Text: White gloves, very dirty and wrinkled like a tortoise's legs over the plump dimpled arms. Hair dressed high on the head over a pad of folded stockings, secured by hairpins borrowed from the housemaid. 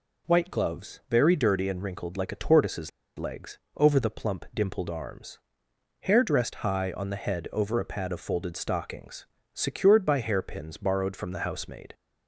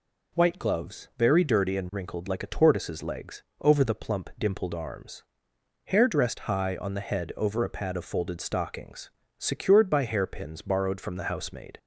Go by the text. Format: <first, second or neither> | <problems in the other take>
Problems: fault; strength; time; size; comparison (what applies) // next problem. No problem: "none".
second | pauses between "tortoise's" and "legs"; slight; at 2.8 s; 0.29 s long // pauses between "legs" and "over"; slight; at 3.5 s; 0.18 s long; slight in the second